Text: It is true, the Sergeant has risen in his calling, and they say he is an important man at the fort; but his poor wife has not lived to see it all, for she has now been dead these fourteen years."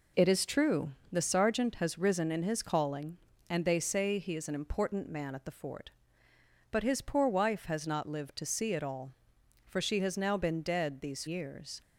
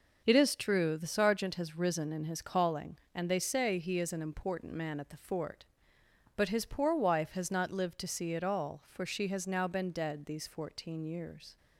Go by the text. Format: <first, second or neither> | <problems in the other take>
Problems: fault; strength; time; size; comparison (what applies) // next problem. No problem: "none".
second | skips "fourteen"; at 11.2 s